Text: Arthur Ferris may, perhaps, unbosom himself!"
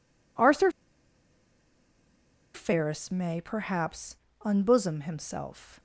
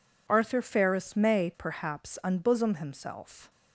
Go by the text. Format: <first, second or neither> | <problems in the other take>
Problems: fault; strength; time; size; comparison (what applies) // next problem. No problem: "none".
second | pauses between "Arthur" and "Ferris"; strong; at 0.7 s; 1.8 s long